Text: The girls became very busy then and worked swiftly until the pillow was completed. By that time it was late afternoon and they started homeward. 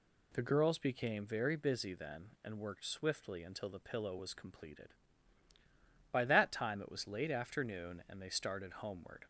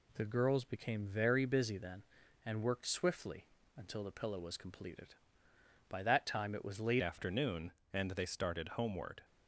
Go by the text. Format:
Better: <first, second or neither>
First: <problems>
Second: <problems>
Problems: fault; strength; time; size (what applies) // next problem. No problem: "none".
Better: first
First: none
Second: pauses between "swiftly" and "until"; slight; at 3.4 s; 0.28 s long // changes voice at "afternoon"; from 7.0 s on; 2.2 s long